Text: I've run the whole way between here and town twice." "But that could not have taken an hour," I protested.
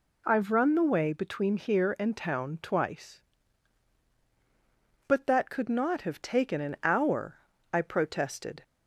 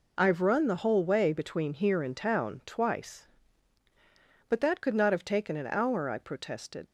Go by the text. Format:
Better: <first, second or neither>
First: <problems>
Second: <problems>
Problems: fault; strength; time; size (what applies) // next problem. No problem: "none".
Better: second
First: skips "whole"; at 0.8 s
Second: none